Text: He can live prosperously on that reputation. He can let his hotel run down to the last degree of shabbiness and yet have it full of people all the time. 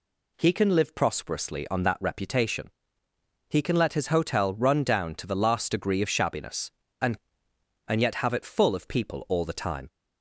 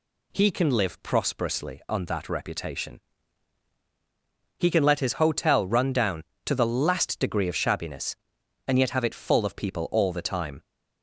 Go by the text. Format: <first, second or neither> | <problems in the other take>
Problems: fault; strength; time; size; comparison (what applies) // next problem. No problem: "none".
second | says "and" twice; at 7.8 s